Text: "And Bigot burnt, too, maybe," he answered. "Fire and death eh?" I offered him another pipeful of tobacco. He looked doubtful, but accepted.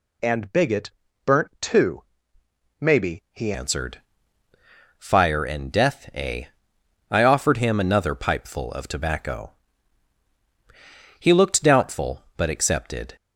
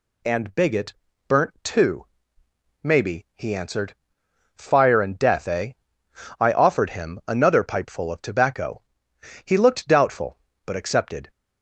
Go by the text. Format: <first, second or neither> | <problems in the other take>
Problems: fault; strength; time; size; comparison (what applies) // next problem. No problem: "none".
second | pauses between "Bigot" and "burnt"; at 0.8 s; 0.38 s long; also in the second // changes voice at "answered"; from 3.5 s on; 9.6 s long